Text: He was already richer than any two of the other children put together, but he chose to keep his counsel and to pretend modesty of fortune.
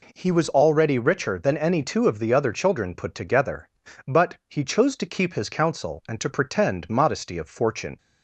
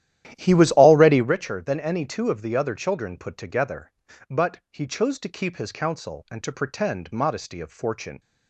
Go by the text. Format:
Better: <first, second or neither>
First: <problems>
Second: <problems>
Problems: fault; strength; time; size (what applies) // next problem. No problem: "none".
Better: first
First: none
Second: starts louder than the rest; strong; until 1.3 s; 12 dB